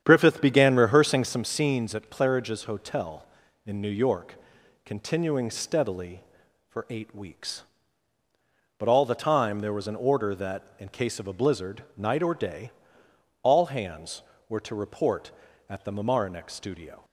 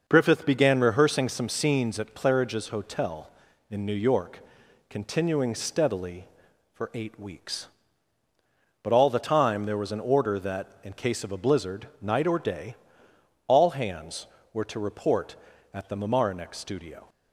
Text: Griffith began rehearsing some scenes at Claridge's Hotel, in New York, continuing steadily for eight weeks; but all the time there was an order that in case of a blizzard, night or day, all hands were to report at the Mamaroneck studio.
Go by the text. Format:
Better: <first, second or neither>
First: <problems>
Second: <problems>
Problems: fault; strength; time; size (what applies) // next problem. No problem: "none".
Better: second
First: starts louder than the rest; strong; until 1.5 s; 9 dB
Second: none